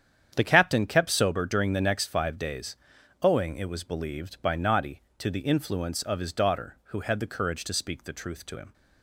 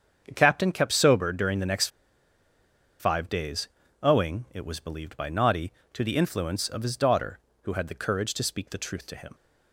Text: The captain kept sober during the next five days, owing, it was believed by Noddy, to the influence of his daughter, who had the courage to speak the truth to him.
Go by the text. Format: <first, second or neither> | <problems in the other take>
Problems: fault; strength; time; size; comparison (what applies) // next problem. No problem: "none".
first | starts louder than the rest; strong; until 1.2 s; 7.5 dB; strong in the first // pauses between "next" and "five"; at 1.8 s; 1.1 s long